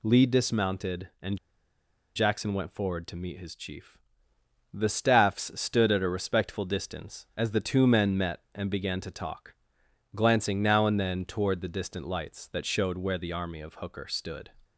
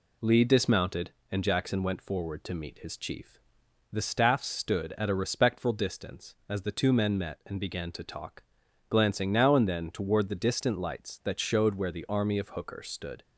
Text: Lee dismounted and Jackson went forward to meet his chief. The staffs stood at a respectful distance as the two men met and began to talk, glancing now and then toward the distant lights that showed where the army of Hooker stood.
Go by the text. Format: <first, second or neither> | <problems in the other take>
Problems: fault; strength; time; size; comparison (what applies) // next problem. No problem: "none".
second | pauses between "and" and "Jackson"; noticeable; at 1.3 s; 0.77 s long